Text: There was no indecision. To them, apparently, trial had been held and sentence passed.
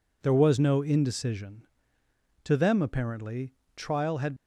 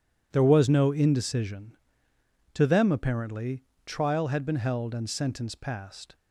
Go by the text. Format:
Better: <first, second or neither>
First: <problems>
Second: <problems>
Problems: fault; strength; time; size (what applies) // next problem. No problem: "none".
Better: second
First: stops before "been held and sentence passed"; at 4.3 s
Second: none